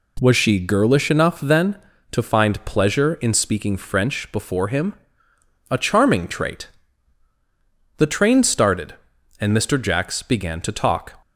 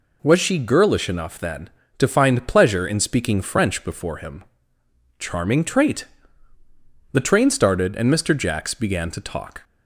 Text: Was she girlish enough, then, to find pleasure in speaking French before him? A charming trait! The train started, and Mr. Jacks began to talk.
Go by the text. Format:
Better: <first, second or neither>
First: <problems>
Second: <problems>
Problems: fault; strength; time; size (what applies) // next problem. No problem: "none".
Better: first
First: none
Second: skips "A"; at 4.8 s